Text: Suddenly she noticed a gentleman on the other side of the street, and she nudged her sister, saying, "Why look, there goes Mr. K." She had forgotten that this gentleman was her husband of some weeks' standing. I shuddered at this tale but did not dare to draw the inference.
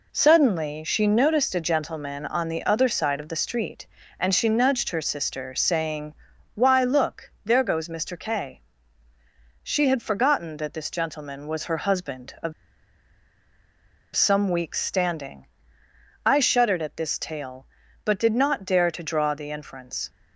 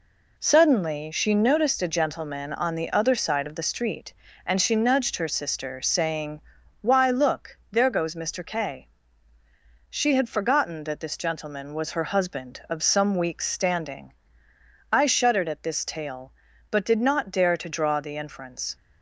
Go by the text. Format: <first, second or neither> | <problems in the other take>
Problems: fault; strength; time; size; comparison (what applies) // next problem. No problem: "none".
second | pauses between "of" and "some"; strong; at 12.5 s; 1.6 s long